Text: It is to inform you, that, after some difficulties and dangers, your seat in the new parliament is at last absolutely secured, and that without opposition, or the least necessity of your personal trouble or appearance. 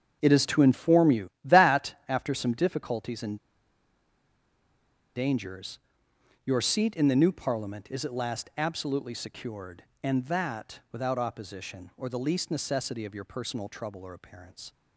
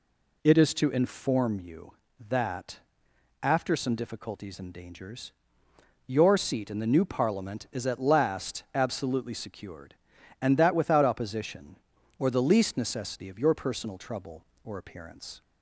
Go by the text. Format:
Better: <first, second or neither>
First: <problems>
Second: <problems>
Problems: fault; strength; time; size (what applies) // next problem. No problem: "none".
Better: second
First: starts louder than the rest; strong; until 1.2 s; 7 dB // pauses between "and" and "dangers"; strong; at 3.3 s; 1.7 s long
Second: none